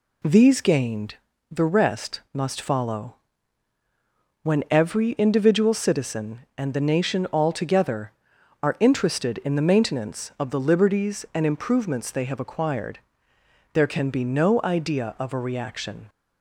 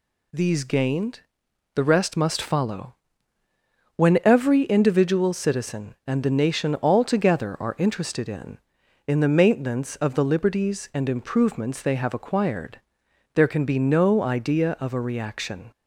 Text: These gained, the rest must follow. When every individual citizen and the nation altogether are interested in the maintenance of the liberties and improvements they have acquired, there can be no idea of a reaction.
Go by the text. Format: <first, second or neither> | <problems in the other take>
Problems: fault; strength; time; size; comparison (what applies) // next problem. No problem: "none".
first | says "in" twice; at 9.0 s